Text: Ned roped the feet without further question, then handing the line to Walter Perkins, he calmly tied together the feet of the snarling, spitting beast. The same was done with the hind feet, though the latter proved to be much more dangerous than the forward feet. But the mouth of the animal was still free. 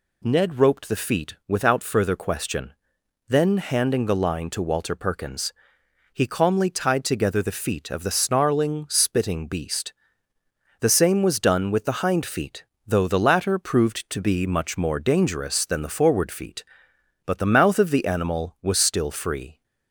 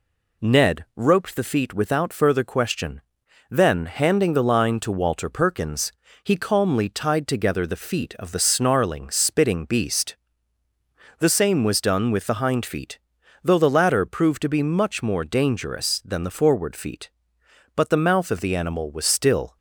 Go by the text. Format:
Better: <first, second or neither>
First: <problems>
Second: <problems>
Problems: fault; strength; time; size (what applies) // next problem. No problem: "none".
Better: first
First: none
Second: stops before "free"; at 19.5 s